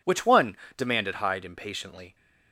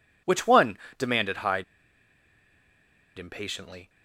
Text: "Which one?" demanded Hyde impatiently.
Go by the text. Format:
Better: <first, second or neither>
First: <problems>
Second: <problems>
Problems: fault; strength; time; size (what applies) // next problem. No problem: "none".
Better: first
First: none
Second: pauses between "Hyde" and "impatiently"; strong; at 1.6 s; 1.5 s long